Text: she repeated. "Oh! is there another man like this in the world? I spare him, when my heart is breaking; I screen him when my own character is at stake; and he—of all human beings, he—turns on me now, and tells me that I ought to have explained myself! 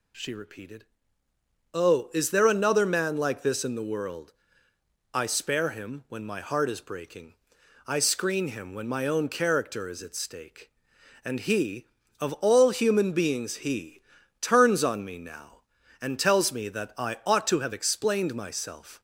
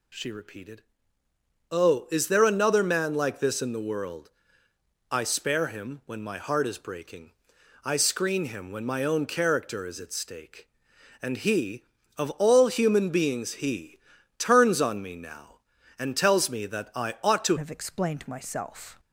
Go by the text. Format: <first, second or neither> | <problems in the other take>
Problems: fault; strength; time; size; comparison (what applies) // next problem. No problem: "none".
first | changes voice at "have"; from 17.5 s on; 1.4 s long